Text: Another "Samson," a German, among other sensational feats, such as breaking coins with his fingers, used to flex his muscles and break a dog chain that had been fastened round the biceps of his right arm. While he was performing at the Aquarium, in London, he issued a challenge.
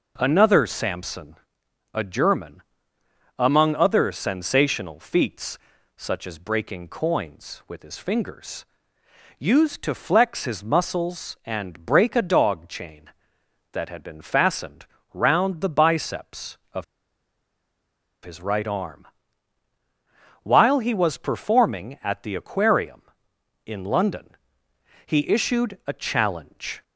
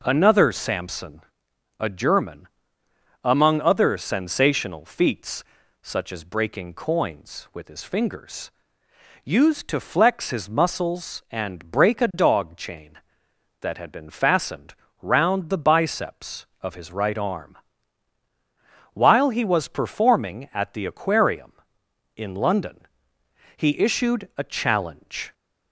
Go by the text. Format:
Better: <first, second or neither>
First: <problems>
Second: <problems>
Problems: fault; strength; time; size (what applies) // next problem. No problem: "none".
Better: second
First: pauses between "fastened" and "round"; slight; at 14.8 s; 0.26 s long // pauses between "of" and "his"; strong; at 16.8 s; 1.3 s long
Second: pauses between "fastened" and "round"; slight; at 14.7 s; 0.26 s long